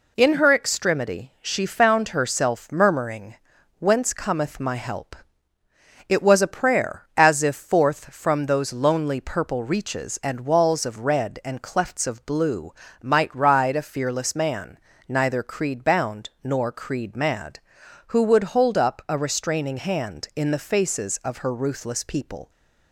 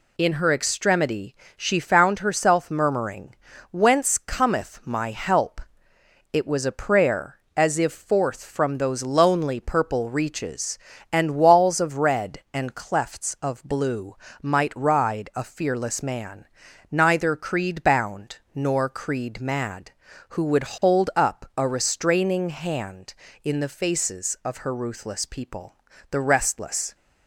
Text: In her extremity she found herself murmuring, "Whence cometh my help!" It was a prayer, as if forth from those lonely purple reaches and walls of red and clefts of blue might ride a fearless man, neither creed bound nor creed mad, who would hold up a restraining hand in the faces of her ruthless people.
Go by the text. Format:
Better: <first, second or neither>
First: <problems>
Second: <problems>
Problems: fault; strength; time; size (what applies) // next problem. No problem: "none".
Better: first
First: pauses between "blue" and "might"; slight; at 12.7 s; 0.30 s long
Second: pauses between "extremity" and "she"; slight; at 1.3 s; 0.22 s long // pauses between "blue" and "might"; slight; at 14.1 s; 0.28 s long // pauses between "bound" and "nor"; slight; at 18.3 s; 0.16 s long // goes on to say "The restless"; noticeable; from 26.1 s on; 0.84 s long